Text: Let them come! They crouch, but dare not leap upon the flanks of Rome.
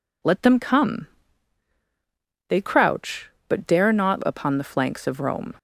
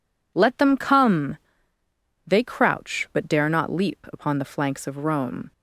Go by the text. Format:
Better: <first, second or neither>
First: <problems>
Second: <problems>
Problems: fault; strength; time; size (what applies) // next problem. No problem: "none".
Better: second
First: skips "leap"; at 4.2 s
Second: none